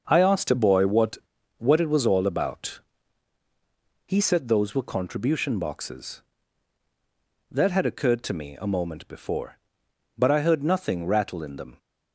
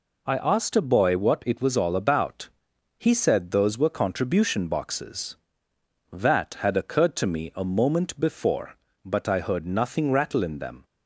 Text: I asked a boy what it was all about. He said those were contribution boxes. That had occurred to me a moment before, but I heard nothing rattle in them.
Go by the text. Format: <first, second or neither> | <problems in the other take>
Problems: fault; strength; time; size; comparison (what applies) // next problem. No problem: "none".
second | starts louder than the rest; until 1.0 s; 6.5 dB // says "what" twice; at 1.5 s